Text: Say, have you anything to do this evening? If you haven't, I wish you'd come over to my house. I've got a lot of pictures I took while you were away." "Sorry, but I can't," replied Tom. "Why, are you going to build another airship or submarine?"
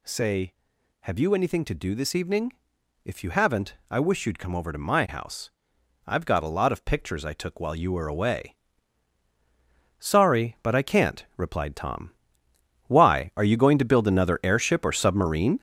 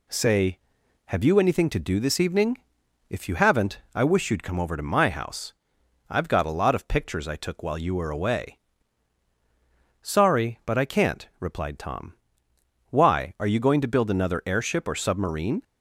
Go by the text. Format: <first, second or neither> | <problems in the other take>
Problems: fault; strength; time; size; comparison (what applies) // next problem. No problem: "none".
second | gets louder; throughout; 6.5 dB